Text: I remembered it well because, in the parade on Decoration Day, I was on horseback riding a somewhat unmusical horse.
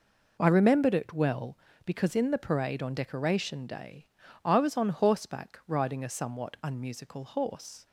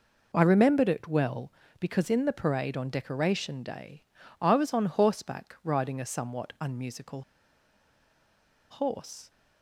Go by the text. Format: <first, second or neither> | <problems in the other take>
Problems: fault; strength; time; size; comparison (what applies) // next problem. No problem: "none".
first | pauses between "unmusical" and "horse"; strong; at 7.2 s; 1.4 s long